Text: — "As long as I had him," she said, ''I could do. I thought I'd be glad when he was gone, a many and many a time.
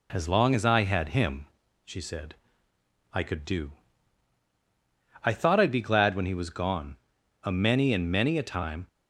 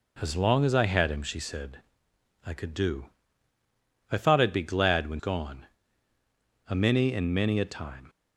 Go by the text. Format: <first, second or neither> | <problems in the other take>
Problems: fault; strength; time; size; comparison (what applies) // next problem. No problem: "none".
first | skips "he was"; at 5.1 s